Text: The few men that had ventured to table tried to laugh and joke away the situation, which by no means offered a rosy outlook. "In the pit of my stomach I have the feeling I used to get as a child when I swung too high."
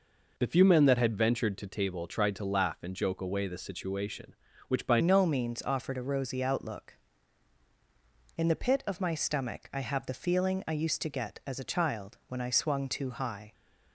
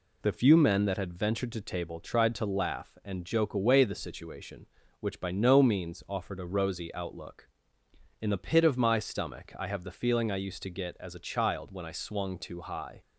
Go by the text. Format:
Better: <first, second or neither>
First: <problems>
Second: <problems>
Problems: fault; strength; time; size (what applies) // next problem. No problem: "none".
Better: second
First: changes voice at "no"; from 4.9 s on; 8.6 s long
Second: none